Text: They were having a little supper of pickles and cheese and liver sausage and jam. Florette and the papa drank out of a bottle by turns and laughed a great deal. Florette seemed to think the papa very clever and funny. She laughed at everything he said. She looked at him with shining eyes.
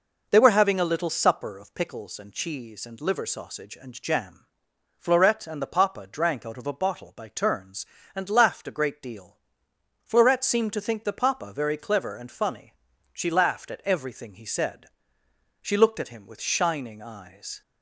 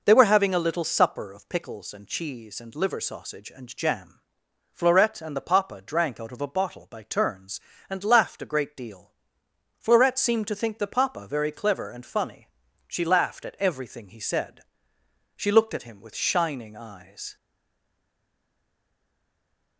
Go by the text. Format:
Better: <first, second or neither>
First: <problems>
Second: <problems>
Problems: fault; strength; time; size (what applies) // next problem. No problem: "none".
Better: first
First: none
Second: stays silent after the last word; from 17.3 s on; 2.4 s long